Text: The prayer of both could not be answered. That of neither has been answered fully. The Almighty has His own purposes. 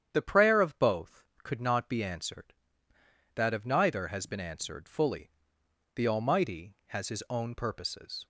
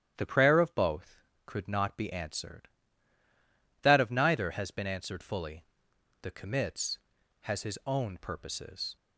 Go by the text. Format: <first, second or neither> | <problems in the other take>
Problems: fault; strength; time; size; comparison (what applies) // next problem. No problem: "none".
first | starts louder than the rest; strong; until 1.2 s; 10.5 dB; strong in the first // says "Commits" for "Almighty"; at 6.3 s